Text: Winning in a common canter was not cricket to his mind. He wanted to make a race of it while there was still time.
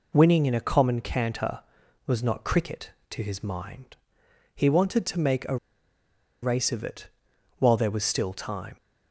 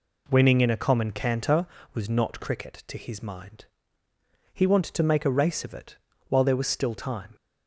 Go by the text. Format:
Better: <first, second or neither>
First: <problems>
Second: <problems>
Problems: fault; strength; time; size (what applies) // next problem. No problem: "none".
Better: second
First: pauses between "a" and "race"; noticeable; at 5.5 s; 0.86 s long // pauses between "it" and "while"; noticeable; at 7.0 s; 0.50 s long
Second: pauses between "it" and "while"; slight; at 5.9 s; 0.32 s long